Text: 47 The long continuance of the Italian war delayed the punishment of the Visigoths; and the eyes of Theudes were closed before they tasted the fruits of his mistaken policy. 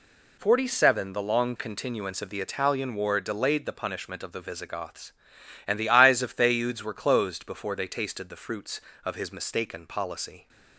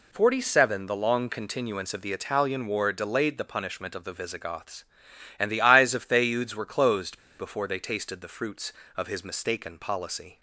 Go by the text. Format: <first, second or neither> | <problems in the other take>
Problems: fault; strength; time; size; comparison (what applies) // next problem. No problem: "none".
first | pauses between "closed" and "before"; slight; at 7.1 s; 0.21 s long